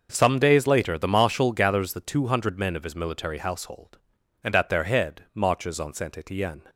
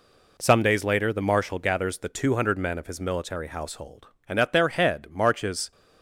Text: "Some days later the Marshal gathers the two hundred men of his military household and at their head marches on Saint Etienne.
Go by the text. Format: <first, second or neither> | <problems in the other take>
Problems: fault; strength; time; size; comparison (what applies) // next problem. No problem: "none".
first | stops before "on Saint Etienne"; at 5.7 s